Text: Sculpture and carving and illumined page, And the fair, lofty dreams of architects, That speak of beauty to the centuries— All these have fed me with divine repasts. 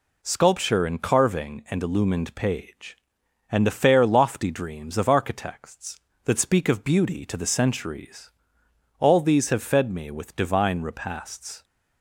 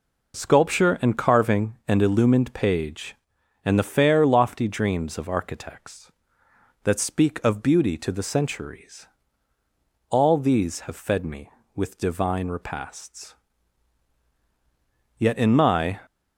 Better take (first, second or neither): first